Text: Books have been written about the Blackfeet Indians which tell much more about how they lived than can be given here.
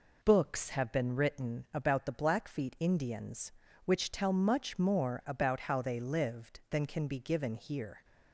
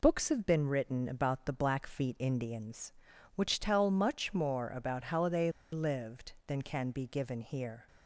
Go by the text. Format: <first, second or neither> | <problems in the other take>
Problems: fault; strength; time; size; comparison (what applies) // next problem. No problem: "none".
first | pauses between "they" and "lived"; slight; at 5.5 s; 0.21 s long